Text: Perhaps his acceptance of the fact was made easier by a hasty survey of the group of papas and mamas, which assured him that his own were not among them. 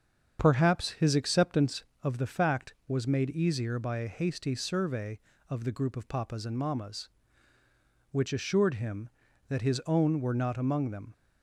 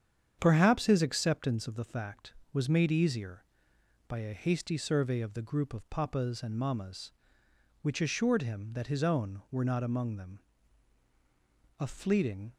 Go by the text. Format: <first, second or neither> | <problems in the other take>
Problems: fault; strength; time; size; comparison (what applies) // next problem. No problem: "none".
first | starts louder than the rest; strong; until 1.4 s; 8 dB; strong in the first // goes on to say "A fleeting"; noticeable; from 11.7 s on; 0.76 s long